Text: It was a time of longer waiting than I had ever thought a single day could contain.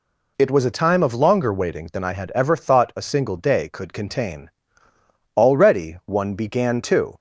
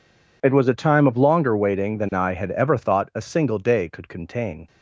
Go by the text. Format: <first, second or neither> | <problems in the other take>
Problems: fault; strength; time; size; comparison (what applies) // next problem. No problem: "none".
second | goes on to say "Already one began to"; strong; from 5.4 s on; 1.6 s long